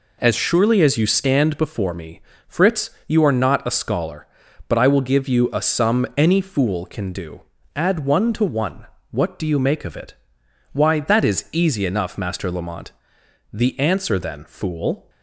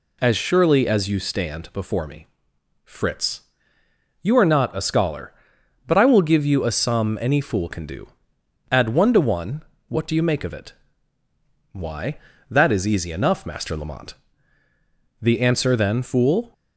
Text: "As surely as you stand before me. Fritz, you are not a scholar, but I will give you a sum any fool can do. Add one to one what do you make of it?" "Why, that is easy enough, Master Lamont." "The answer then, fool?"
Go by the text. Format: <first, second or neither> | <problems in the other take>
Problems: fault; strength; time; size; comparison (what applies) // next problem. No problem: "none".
neither | pauses between "one" and "what"; slight; the same in both